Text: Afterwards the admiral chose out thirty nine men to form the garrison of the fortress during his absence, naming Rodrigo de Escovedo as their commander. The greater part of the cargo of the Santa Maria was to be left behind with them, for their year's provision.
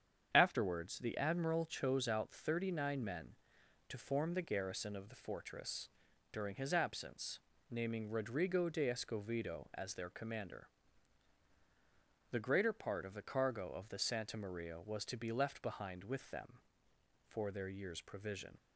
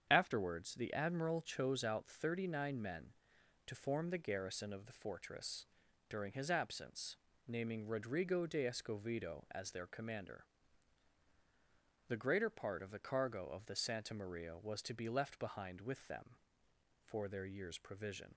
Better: neither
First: starts louder than the rest; strong; until 1.3 s; 8 dB // pauses between "fortress" and "during"; noticeable; at 5.8 s; 0.46 s long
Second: starts louder than the rest; strong; until 1.1 s; 8 dB // pauses between "fortress" and "during"; noticeable; at 5.6 s; 0.46 s long

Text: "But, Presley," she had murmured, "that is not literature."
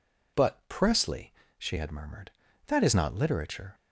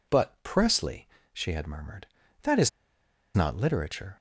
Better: first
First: none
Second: pauses between "is" and "not"; noticeable; at 2.6 s; 0.66 s long

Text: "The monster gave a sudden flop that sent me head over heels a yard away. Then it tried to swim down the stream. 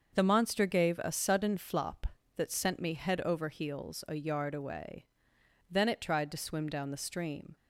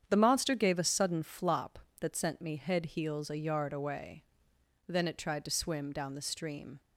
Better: first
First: starts louder than the rest; until 1.1 s; 6.5 dB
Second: starts louder than the rest; strong; until 1.1 s; 8.5 dB // skips "over"; at 2.8 s

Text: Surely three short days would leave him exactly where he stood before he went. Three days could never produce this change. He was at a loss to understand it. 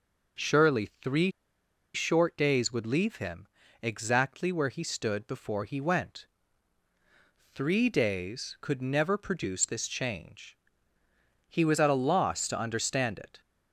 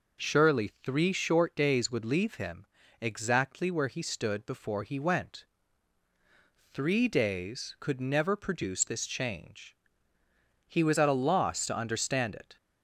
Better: second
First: pauses between "three" and "short"; noticeable; at 1.3 s; 0.63 s long // pauses between "him" and "exactly"; slight; at 3.4 s; 0.34 s long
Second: pauses between "him" and "exactly"; slight; at 2.6 s; 0.34 s long

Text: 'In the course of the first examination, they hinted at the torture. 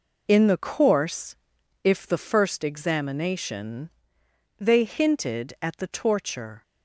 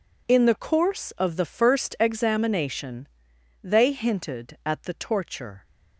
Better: second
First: says "if" for "of"; at 1.8 s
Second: none

